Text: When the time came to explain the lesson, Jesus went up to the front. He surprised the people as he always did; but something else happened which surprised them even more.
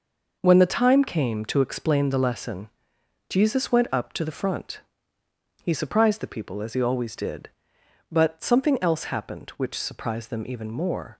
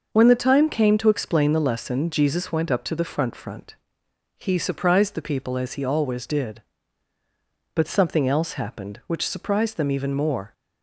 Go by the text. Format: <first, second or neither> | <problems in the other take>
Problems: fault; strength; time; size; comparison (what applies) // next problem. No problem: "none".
first | starts louder than the rest; noticeable; until 1.1 s; 6 dB // says "front" twice; at 3.3 s